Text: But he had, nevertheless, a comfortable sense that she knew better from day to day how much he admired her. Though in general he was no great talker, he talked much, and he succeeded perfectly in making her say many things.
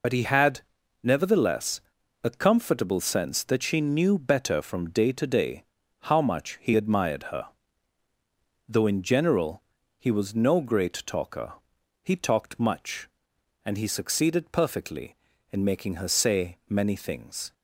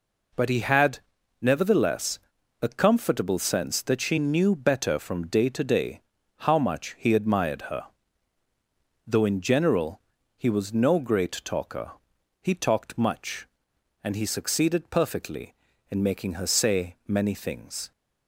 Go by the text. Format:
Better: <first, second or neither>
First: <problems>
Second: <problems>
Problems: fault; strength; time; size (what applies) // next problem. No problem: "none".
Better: second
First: loses the start of "But"; at 0.0 s; 70 ms // pauses between "day" and "how"; at 5.6 s; 0.38 s long // pauses between "general" and "he"; at 9.6 s; 0.38 s long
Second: pauses between "day" and "how"; at 6.0 s; 0.38 s long // pauses between "general" and "he"; at 9.9 s; 0.38 s long